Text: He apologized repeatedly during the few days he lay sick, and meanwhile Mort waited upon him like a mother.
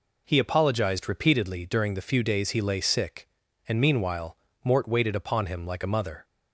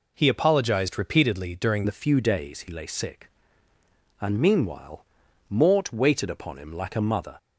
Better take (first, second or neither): first